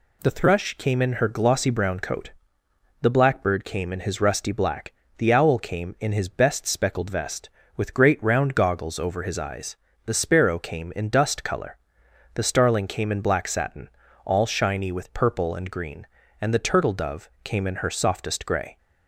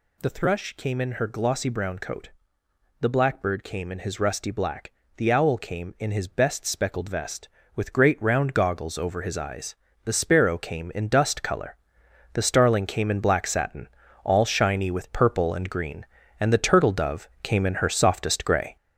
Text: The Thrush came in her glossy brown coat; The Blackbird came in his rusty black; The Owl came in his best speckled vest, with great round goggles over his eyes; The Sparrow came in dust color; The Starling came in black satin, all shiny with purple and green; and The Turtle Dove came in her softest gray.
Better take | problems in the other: first | gets louder; noticeable; throughout; 6 dB // pauses between "Dove" and "came"; slight; at 17.2 s; 0.16 s long; slight in the first

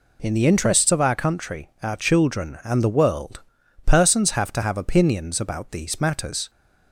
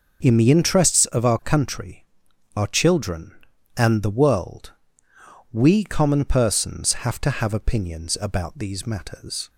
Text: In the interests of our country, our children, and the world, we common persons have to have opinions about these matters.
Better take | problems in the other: second | skips "we common"; at 3.6 s

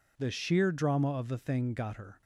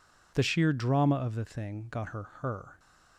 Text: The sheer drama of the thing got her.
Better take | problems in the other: first | says "her" twice; at 2.4 s

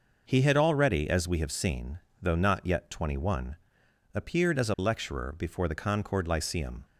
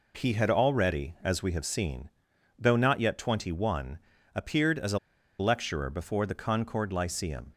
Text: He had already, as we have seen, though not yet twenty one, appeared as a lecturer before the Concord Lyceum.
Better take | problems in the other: first | pauses between "a" and "lecturer"; at 4.9 s; 0.41 s long

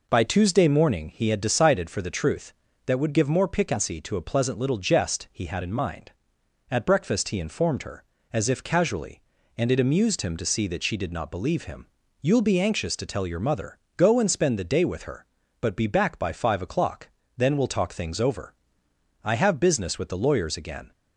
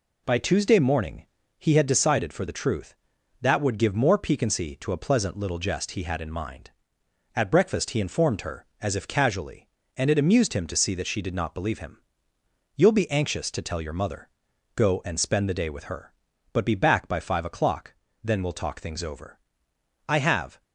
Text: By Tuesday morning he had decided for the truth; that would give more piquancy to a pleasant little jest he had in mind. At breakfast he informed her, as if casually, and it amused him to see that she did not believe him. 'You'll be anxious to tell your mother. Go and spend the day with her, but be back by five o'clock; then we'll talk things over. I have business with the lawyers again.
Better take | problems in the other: first | pauses between "morning" and "he"; slight; at 1.2 s; 0.32 s long // stops before "business with the lawyers again"; at 20.6 s

